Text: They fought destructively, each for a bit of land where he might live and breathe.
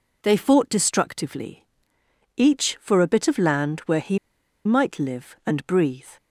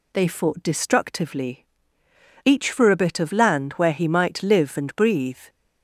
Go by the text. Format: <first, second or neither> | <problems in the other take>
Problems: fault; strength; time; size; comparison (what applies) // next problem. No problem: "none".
second | pauses between "he" and "might"; noticeable; at 4.1 s; 0.48 s long